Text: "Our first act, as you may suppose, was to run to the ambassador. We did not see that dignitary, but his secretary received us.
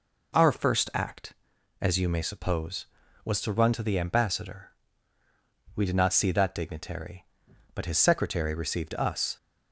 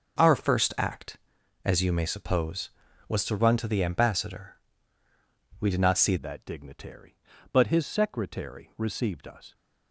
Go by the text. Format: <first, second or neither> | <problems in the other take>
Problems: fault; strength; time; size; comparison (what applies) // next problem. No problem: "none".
first | starts louder than the rest; until 1.6 s; 6.5 dB // changes voice at "that"; from 6.1 s on; 3.4 s long